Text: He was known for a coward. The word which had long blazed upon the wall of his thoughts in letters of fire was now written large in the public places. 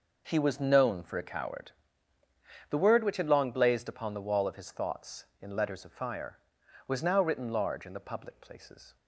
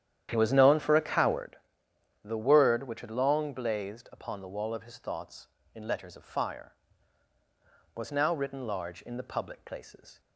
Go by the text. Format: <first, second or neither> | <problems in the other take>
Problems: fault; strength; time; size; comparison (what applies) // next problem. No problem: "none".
first | starts louder than the rest; strong; until 1.5 s; 10.5 dB